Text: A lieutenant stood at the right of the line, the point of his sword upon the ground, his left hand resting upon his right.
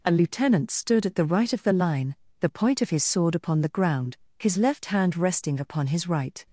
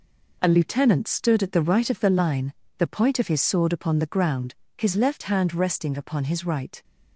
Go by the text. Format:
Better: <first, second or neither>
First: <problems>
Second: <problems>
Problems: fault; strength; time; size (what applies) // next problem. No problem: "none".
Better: first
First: none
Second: gets quieter; strong; throughout; 8.5 dB